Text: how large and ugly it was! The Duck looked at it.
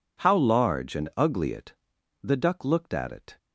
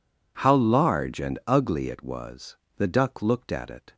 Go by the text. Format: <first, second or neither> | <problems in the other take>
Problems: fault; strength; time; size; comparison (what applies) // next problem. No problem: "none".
second | skips "was"; at 1.9 s